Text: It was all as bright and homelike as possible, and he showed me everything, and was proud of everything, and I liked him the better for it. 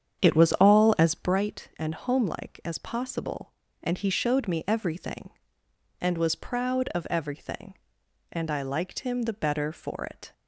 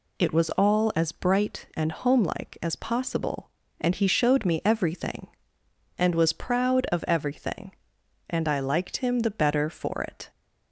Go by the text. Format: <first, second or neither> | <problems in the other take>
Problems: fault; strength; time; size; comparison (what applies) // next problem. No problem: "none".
second | starts louder than the rest; strong; until 1.4 s; 8.5 dB